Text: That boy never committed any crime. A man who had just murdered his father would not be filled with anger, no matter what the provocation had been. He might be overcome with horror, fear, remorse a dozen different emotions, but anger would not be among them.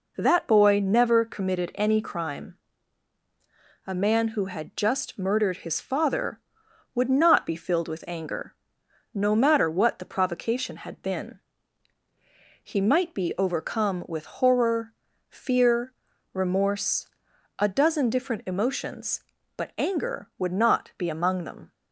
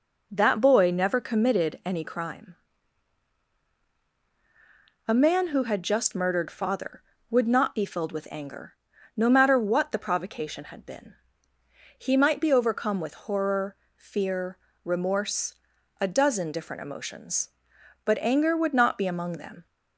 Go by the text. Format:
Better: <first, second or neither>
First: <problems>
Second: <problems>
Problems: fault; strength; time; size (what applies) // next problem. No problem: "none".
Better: first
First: pauses between "remorse" and "a"; noticeable; at 17.0 s; 0.52 s long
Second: skips "his"; at 6.5 s // pauses between "remorse" and "a"; at 15.5 s; 0.44 s long